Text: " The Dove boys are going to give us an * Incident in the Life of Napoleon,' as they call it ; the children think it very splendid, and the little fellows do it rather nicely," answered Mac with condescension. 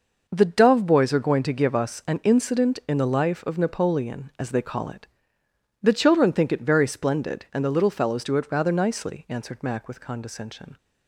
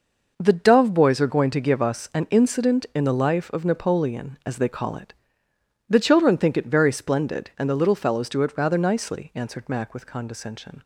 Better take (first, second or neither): neither